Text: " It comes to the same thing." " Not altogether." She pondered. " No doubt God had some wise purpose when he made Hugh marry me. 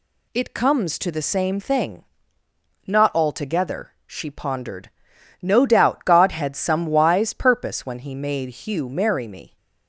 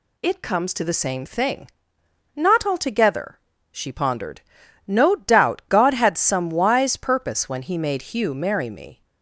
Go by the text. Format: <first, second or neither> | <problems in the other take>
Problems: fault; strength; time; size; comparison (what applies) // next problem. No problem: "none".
neither | none